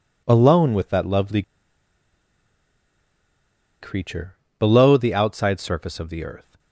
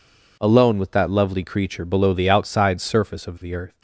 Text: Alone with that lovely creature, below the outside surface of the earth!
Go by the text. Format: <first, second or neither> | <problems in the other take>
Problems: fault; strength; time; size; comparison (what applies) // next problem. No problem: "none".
second | pauses between "lovely" and "creature"; strong; at 1.4 s; 2.3 s long